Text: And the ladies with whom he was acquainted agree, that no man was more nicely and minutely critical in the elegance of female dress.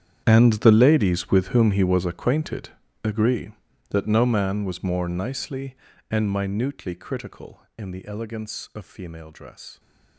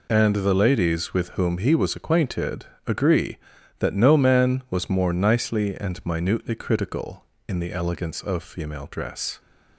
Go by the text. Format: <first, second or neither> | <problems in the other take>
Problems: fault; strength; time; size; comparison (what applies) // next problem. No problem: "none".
second | gets quieter; strong; throughout; 17 dB // pauses between "acquainted" and "agree"; slight; at 2.6 s; 0.34 s long; slight in the second